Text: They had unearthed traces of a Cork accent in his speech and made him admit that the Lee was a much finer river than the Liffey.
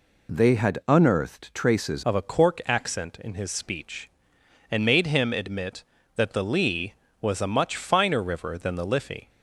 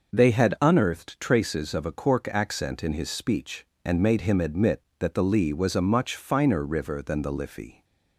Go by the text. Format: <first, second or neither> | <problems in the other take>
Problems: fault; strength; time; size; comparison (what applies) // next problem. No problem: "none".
second | changes voice at "of"; from 2.0 s on; 7.2 s long